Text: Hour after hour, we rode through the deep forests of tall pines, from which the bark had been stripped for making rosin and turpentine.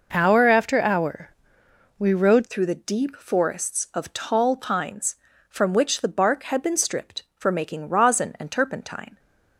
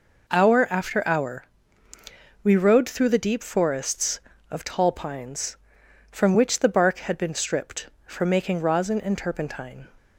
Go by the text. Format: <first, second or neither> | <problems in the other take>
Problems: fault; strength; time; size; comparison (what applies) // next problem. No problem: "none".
second | changes voice at "through"; from 2.4 s on; 6.7 s long